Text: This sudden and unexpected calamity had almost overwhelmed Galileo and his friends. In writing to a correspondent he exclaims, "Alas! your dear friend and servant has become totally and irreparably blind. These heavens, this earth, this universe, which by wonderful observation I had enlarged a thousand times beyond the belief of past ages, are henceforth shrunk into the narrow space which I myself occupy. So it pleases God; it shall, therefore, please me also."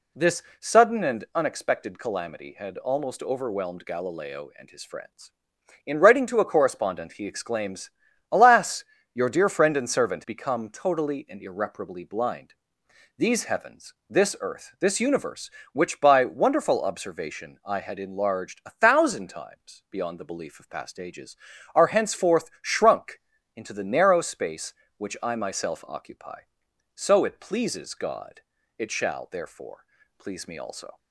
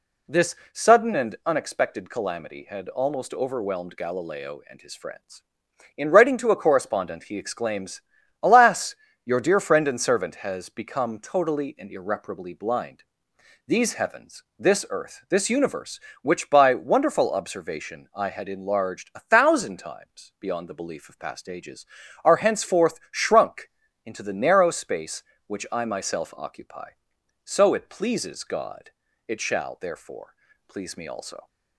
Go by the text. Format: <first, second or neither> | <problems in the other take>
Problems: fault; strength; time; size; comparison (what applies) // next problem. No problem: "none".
second | pauses between "This" and "sudden"; slight; at 0.4 s; 0.16 s long; slight in the second // skips "has"; at 10.2 s // pauses between "shrunk" and "into"; slight; at 23.2 s; 0.36 s long; slight in the second